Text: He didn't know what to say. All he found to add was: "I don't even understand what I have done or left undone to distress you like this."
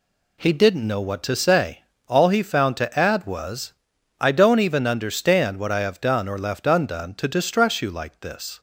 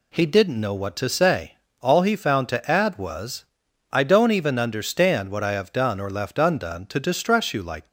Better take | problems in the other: first | stops before "this"; at 7.8 s

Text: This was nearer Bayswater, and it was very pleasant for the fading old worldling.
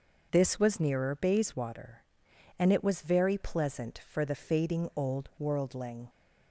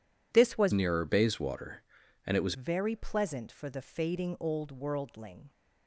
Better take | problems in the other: first | changes voice from "nearer" to "was"; from 0.7 to 2.5 s; 1.8 s long

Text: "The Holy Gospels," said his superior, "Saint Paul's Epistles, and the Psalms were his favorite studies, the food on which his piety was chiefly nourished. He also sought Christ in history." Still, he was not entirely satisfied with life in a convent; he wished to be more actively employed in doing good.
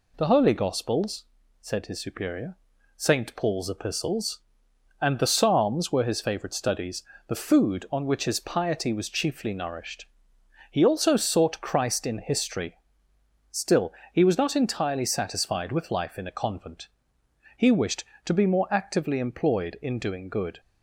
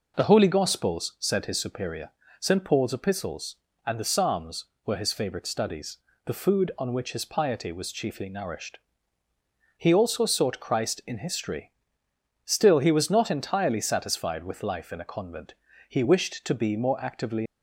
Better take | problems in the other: first | stops before "employed in doing good"; at 17.4 s

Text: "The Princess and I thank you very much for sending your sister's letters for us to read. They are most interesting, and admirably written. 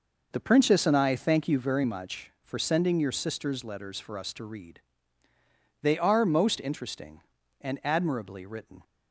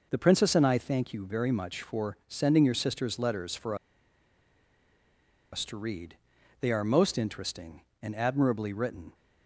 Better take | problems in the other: first | pauses between "for" and "us"; strong; at 3.7 s; 1.7 s long

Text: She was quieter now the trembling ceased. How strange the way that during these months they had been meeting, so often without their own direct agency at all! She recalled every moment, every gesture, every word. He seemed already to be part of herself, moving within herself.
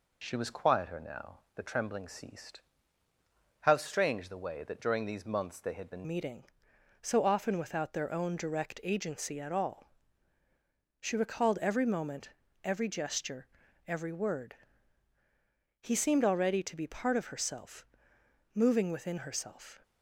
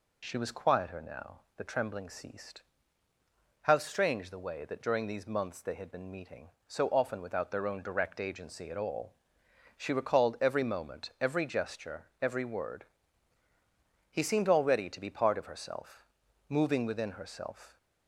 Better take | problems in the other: second | pauses between "now" and "the"; slight; at 1.4 s; 0.16 s long; slight in the second // changes voice at "meeting"; from 6.0 s on; 13.7 s long

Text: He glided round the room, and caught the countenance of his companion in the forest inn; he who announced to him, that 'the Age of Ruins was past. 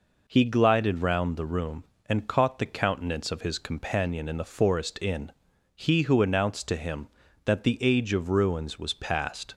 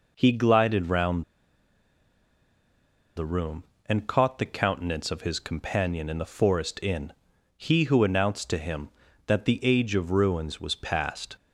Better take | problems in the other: first | pauses between "round" and "the"; strong; at 1.2 s; 1.9 s long

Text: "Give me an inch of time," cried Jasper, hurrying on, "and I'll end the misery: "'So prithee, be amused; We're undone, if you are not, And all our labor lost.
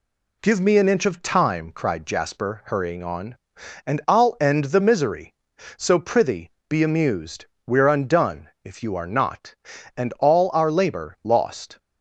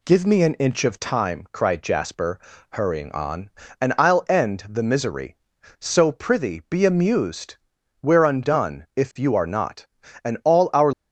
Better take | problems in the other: first | stops before "labor lost"; at 10.9 s

